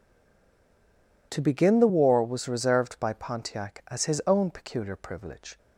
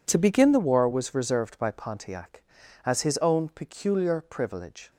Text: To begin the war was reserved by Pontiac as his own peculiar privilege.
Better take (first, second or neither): second